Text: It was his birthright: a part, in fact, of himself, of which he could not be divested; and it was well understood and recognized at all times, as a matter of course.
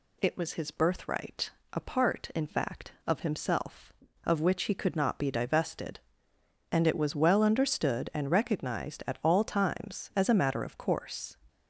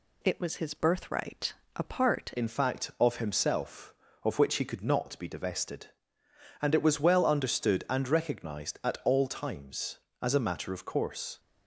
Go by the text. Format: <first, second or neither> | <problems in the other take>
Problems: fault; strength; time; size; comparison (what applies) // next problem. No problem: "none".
first | changes voice at "in"; from 2.3 s on; 9.0 s long